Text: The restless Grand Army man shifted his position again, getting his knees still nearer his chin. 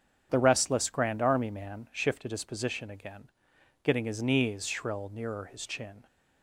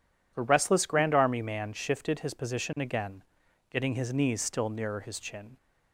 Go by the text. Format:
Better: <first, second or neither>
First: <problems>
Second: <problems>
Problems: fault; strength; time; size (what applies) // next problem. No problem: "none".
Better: second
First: starts louder than the rest; strong; until 1.3 s; 8 dB // says "shrill" for "still"; at 4.6 s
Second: none